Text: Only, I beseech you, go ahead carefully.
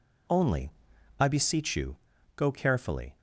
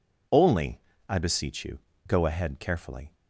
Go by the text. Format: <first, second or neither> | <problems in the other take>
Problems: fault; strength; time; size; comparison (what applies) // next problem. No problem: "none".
second | skips "ahead"; at 2.5 s